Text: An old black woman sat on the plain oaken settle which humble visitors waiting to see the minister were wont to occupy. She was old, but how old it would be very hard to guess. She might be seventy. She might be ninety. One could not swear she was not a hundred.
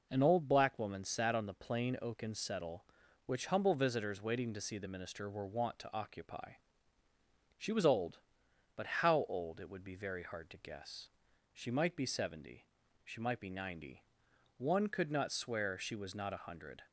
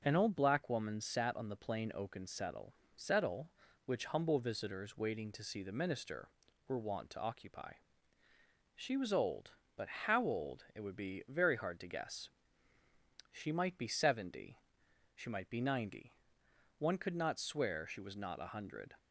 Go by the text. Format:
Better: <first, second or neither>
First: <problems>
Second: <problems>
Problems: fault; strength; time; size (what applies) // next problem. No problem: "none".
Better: first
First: none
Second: says "settle" twice; at 2.9 s // pauses between "but" and "how"; slight; at 9.8 s; 0.16 s long